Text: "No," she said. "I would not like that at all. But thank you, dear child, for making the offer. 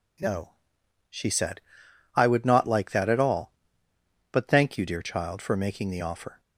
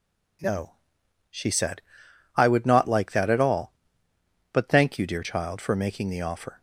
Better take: neither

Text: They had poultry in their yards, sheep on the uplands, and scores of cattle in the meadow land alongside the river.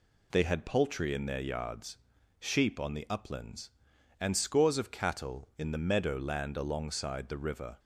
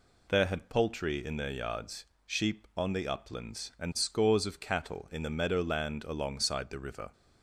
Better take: first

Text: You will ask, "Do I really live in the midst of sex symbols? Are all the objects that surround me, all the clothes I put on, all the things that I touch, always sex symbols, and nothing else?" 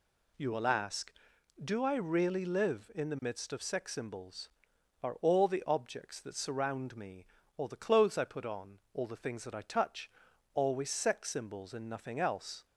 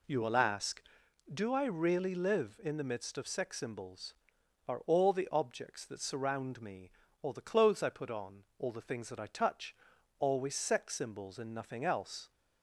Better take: first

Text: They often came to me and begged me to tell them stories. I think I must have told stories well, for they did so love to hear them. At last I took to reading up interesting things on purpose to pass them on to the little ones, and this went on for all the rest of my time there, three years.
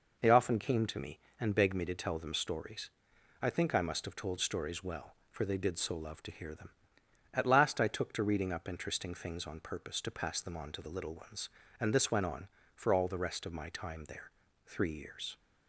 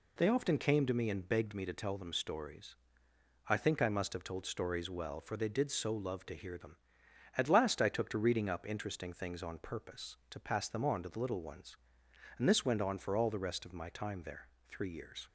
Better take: neither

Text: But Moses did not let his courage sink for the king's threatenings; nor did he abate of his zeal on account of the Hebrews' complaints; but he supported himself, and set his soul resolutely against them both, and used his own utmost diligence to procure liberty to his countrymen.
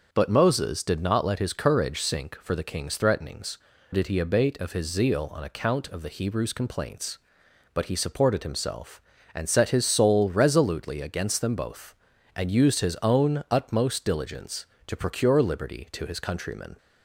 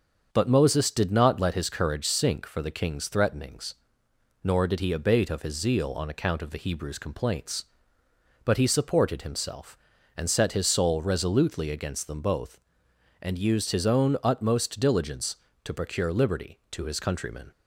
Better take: second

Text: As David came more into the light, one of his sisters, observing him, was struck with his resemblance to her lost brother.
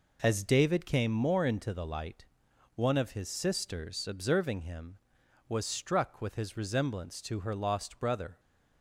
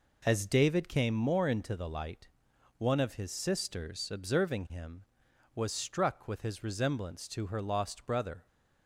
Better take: neither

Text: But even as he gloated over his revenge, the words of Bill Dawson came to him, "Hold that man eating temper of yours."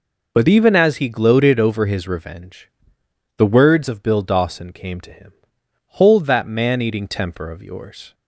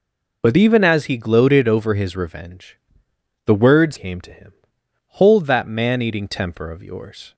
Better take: first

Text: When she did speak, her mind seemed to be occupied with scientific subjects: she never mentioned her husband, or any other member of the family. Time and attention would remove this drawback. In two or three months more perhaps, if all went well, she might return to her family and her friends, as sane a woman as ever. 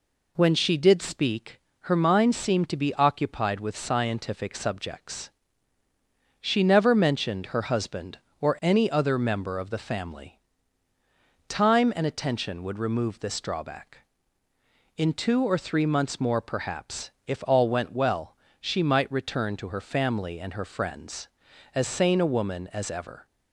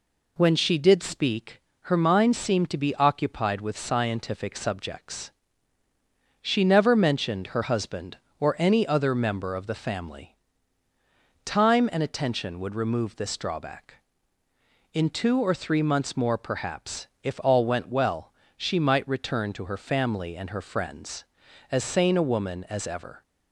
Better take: neither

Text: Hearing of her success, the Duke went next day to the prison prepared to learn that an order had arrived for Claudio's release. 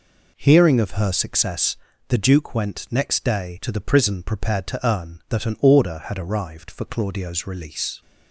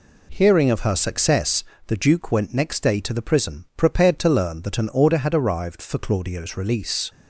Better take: second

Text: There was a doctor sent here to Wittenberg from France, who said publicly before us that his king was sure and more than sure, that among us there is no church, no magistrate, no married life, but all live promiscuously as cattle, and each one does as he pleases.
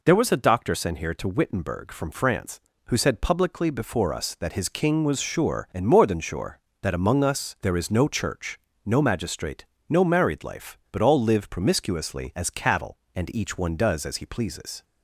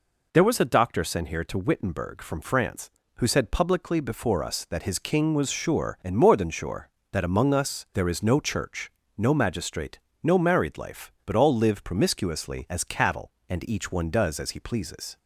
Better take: neither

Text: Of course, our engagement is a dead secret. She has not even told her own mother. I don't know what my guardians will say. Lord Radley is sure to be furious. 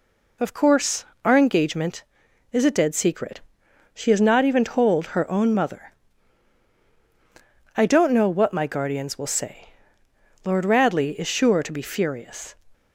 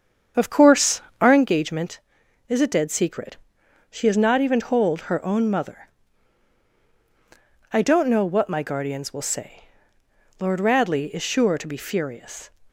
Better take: first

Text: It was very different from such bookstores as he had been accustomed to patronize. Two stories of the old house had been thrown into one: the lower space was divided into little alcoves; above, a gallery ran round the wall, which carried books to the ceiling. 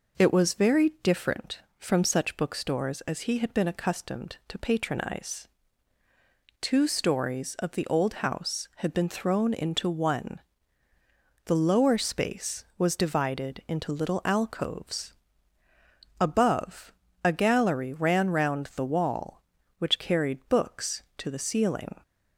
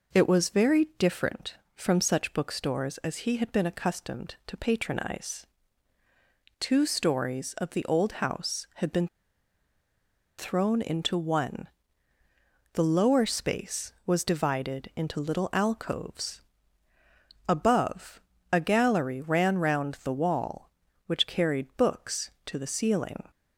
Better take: first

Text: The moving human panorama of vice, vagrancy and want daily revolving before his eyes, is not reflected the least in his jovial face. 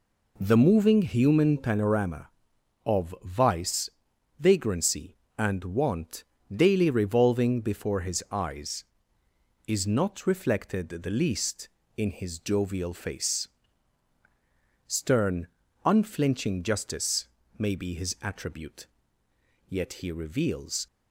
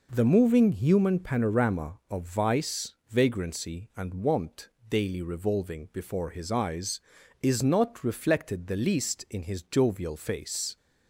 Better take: second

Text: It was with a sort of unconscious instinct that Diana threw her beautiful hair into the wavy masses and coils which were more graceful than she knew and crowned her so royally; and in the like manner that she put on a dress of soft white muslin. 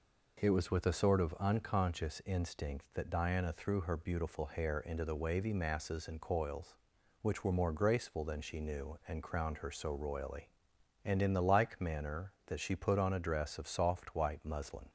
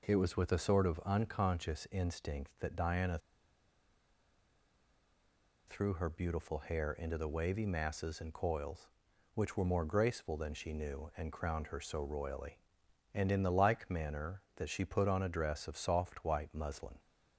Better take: first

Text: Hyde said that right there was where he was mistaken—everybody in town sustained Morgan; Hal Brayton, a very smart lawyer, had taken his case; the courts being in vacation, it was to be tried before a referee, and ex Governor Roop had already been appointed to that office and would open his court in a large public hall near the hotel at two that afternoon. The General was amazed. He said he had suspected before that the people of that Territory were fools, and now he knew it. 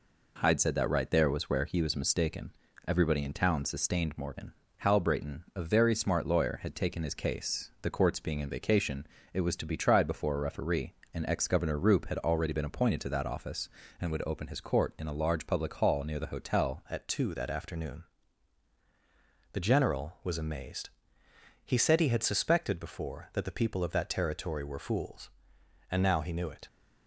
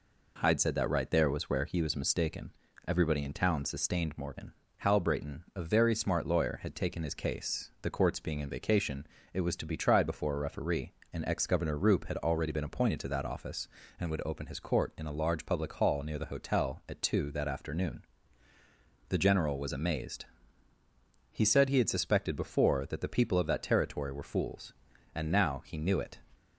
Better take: second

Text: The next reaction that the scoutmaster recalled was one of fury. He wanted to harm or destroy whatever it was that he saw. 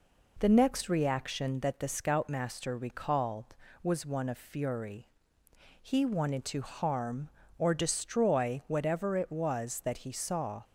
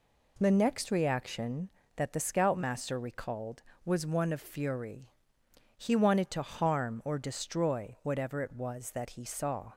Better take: neither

